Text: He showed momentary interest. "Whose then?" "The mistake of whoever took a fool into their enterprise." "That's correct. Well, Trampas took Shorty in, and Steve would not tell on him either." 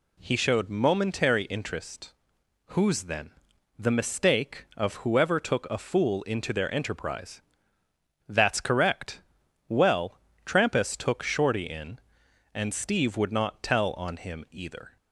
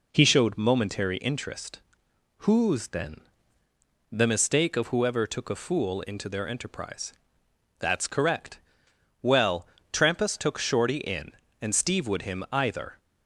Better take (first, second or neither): first